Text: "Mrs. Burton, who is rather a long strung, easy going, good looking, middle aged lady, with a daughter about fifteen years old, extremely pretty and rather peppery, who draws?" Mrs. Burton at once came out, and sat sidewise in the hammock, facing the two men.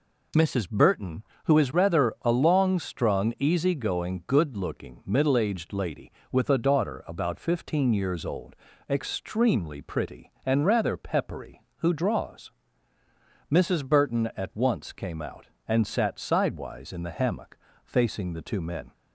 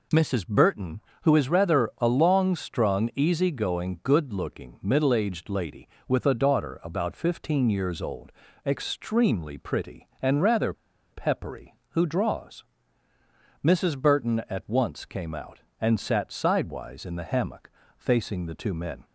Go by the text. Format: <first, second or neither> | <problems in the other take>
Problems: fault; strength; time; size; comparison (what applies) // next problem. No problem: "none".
first | pauses between "rather" and "peppery"; at 10.7 s; 0.39 s long